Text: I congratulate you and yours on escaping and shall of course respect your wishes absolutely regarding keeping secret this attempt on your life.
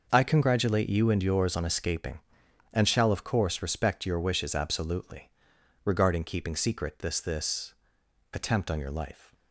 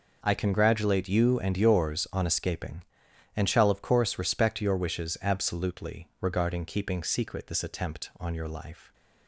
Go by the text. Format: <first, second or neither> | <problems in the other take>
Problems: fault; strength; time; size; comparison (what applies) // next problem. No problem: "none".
second | pauses between "absolutely" and "regarding"; noticeable; at 5.3 s; 0.52 s long // says "this" twice; at 7.1 s